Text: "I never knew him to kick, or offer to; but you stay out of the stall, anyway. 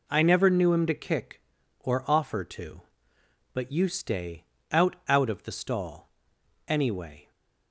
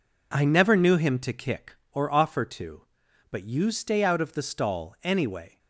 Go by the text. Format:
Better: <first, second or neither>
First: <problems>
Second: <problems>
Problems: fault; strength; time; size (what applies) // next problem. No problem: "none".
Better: second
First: pauses between "stay" and "out"; slight; at 4.4 s; 0.26 s long // says "out" twice; at 5.0 s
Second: none